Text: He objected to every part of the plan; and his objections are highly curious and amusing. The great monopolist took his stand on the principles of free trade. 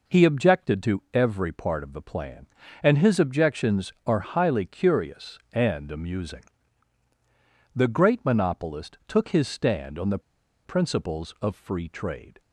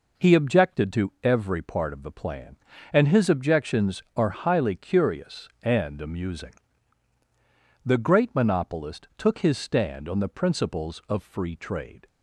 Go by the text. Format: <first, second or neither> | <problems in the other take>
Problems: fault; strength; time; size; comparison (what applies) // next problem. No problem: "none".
second | pauses between "the" and "principles"; at 10.1 s; 0.45 s long